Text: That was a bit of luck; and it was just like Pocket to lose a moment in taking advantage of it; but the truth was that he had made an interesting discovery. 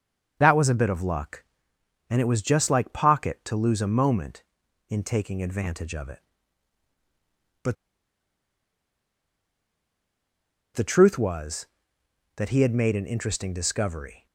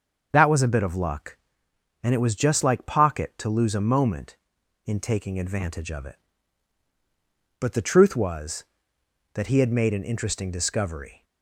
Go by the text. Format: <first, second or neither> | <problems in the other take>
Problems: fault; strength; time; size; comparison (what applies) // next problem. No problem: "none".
second | starts louder than the rest; until 1.4 s; 6.5 dB; also in the second // pauses between "but" and "the"; strong; at 7.7 s; 3.0 s long